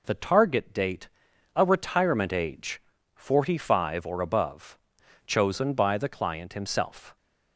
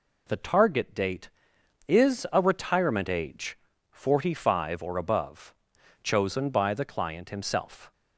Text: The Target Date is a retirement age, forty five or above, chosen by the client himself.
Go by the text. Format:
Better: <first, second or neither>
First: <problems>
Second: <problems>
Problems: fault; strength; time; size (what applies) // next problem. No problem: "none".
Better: second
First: skips "is"; at 1.3 s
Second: none